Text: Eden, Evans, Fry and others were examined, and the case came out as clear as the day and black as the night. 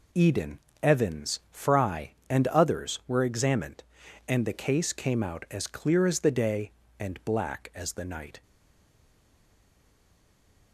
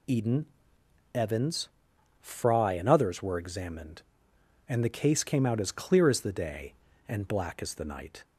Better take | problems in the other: second | stays silent after the last word; from 8.4 s on; 2.3 s long

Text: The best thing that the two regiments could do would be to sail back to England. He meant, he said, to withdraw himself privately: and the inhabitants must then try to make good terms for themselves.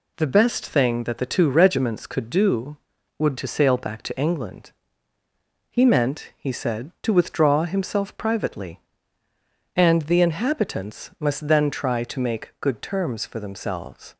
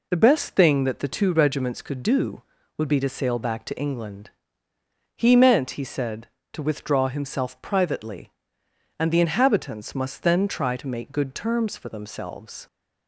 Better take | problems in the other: second | skips "be"; at 3.3 s

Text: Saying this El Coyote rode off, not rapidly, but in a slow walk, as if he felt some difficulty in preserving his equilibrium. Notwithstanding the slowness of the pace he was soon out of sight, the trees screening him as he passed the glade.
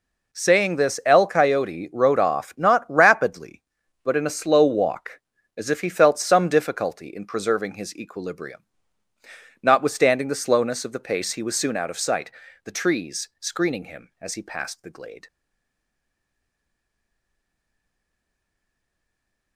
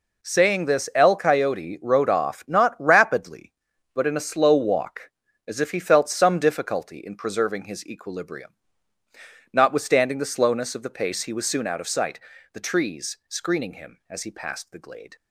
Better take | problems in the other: second | stays silent after the last word; strong; from 15.2 s on; 4.3 s long

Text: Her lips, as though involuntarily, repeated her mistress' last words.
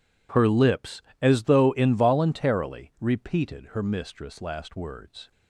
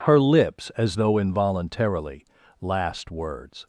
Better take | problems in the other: first | skips "repeated her mistress"; at 2.4 s

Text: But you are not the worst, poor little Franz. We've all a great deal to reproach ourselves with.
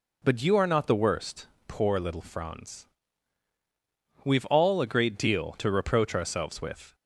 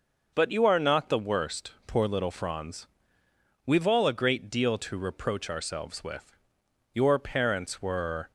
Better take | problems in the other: first | goes on to say "Your parents were"; from 6.9 s on; 1.3 s long

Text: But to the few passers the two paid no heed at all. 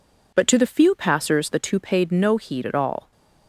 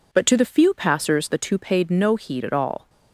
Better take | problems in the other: neither | none

